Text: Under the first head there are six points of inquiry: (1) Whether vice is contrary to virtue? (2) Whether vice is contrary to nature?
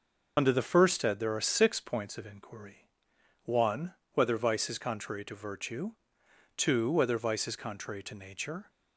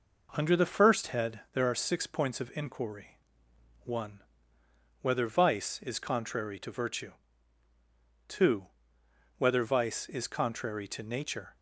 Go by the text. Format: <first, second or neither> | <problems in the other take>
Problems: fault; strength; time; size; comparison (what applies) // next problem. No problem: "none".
second | loses the start of "Under"; at 0.3 s; 40 ms